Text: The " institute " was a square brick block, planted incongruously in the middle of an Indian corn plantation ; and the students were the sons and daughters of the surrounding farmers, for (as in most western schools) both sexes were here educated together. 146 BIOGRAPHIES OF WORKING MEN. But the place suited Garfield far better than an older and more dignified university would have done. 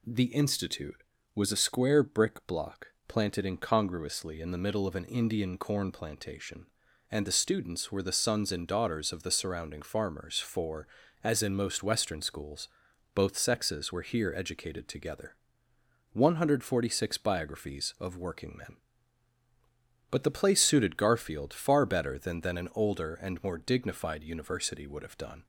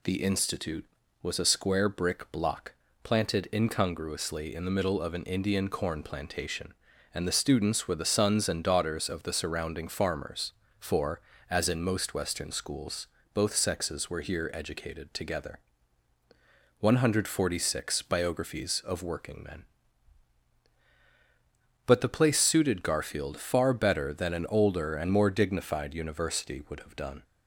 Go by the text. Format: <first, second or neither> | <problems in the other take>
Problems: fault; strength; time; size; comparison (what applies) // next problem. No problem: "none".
second | says "than" twice; at 22.4 s